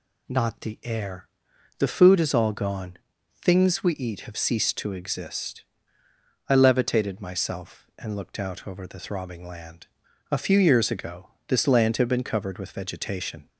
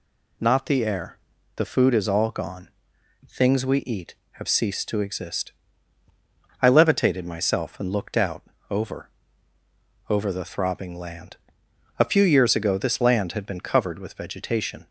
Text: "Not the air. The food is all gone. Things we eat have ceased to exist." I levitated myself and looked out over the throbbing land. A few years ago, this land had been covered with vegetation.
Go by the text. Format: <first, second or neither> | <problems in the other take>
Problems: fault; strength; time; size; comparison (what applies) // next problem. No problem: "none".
first | pauses between "out" and "over"; slight; at 8.4 s; 0.28 s long // says "over" twice; at 10.0 s